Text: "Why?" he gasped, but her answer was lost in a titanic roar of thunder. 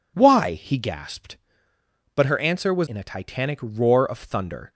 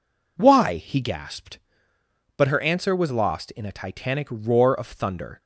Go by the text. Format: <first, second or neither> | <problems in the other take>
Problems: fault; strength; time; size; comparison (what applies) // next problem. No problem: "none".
second | skips "lost"; at 2.8 s